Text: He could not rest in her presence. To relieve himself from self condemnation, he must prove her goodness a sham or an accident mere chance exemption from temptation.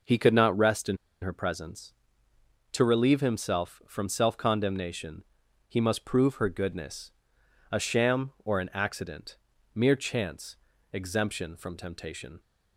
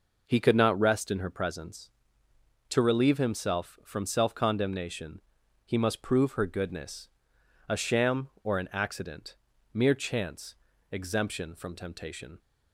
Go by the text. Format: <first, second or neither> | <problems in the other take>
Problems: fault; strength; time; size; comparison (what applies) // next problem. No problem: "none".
second | pauses between "in" and "her"; slight; at 0.9 s; 0.24 s long // pauses between "goodness" and "a"; noticeable; at 7.0 s; 0.62 s long; noticeable in the second // pauses between "accident" and "mere"; slight; at 9.3 s; 0.36 s long; slight in the second // pauses between "chance" and "exemption"; at 10.5 s; 0.38 s long; also in the second